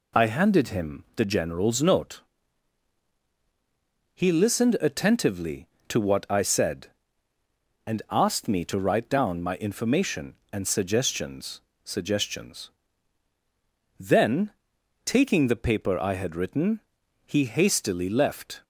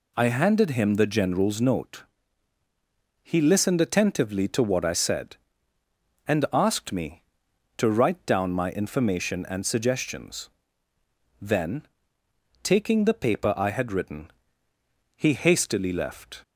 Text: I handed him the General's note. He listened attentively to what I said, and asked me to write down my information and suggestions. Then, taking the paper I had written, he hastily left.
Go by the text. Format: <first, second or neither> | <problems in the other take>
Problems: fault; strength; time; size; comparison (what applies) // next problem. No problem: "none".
second | says "suggestions" twice; at 11.8 s